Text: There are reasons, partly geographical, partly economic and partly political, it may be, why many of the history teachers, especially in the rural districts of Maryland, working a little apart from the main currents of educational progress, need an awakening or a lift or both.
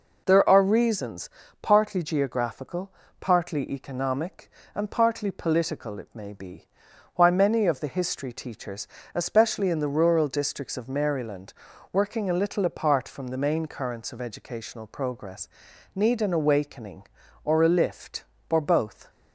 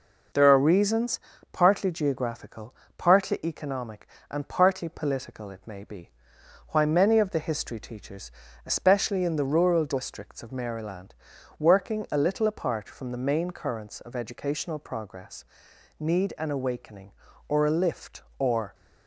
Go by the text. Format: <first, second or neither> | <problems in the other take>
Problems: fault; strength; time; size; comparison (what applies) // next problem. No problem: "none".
first | stops before "both"; at 18.7 s